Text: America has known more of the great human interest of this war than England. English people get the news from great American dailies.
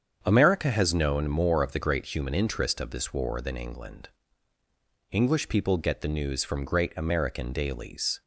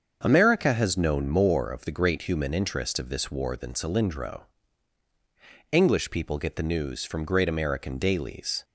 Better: first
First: starts louder than the rest; strong; until 1.2 s; 7.5 dB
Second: starts louder than the rest; until 1.2 s; 7 dB // says "Cylindro" for "England"; at 3.7 s

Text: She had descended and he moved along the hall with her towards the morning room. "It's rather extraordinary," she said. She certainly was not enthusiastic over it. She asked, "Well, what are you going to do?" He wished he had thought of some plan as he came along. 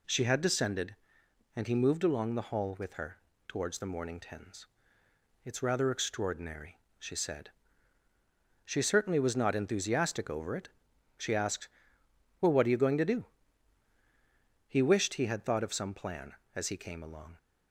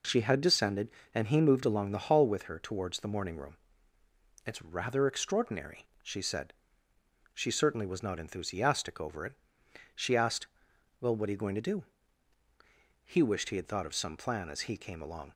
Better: second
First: pauses between "her" and "towards"; slight; at 3.1 s; 0.30 s long // says "tens" for "room"; at 4.1 s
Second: none

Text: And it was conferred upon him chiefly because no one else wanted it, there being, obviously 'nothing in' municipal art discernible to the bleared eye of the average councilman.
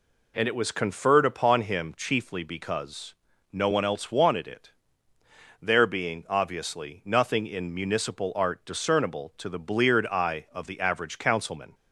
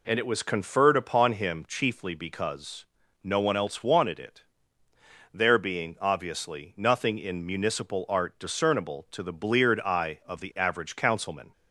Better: neither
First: pauses between "because" and "no"; at 3.1 s; 0.38 s long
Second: pauses between "because" and "no"; at 2.8 s; 0.38 s long

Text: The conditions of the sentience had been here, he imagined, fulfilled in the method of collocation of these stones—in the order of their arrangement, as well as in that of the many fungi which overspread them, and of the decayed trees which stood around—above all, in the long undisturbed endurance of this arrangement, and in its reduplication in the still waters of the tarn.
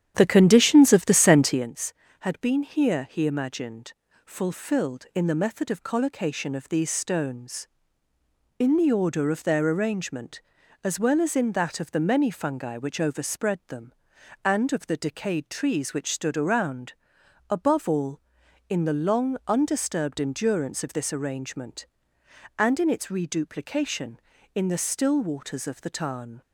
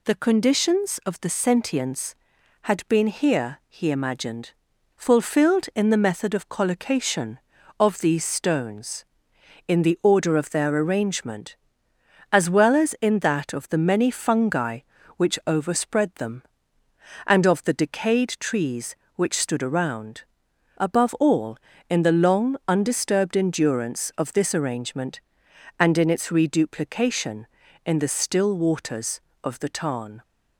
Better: second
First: starts louder than the rest; strong; until 1.7 s; 10 dB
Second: none

